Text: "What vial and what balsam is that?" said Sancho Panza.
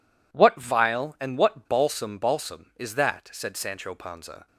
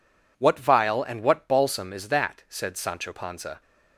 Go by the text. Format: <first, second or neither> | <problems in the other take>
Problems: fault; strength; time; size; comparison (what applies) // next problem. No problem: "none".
second | says "balsam" twice; at 2.1 s